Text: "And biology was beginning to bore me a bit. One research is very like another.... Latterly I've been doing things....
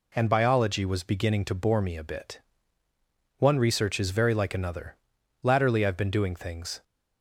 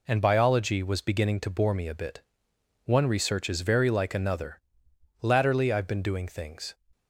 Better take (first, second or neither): neither